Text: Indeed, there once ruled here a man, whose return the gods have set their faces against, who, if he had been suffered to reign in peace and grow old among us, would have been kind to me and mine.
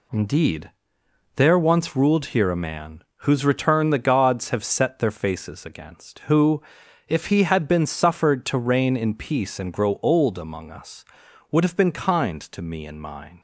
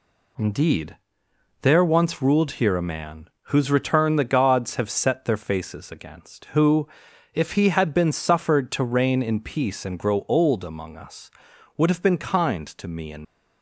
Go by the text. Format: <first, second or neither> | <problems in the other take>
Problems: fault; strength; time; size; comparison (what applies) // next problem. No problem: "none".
first | stops before "mine"; at 13.2 s